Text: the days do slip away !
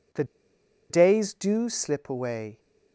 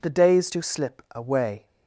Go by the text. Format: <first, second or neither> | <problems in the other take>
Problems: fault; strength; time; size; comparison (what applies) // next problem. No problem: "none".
second | pauses between "the" and "days"; noticeable; at 0.2 s; 0.66 s long